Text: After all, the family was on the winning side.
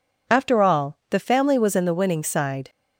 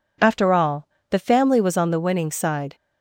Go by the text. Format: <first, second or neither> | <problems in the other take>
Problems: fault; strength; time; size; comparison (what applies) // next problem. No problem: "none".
second | says "in" for "on"; at 1.7 s